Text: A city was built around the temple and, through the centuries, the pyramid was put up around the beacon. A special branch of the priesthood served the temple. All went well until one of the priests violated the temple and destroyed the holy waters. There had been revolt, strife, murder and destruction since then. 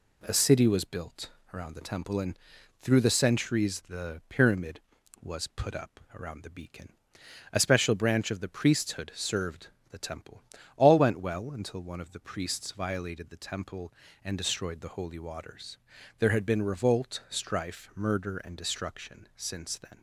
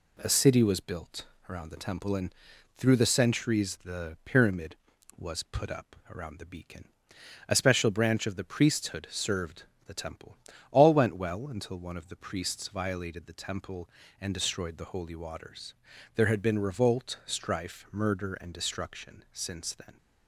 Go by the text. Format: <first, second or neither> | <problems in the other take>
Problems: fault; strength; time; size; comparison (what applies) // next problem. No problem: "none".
neither | pauses between "built" and "around"; slight; the same in both // pauses between "up" and "around"; slight; the same in both // pauses between "served" and "the"; slight; the same in both